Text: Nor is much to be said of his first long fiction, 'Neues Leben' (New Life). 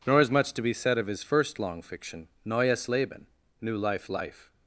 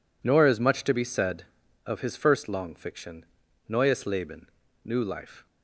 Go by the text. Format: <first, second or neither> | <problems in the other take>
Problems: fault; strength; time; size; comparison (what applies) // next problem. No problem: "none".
second | says "Life" twice; at 4.0 s